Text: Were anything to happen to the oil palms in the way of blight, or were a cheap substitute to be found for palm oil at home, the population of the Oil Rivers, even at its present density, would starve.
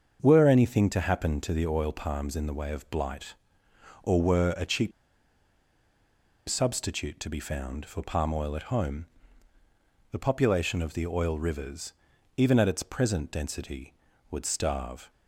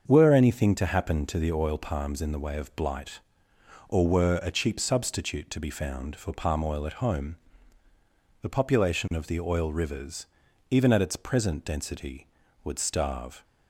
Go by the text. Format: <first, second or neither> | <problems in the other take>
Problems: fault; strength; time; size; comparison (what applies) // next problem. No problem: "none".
second | starts louder than the rest; until 1.2 s; 7 dB; also in the second // pauses between "cheap" and "substitute"; strong; at 4.9 s; 1.5 s long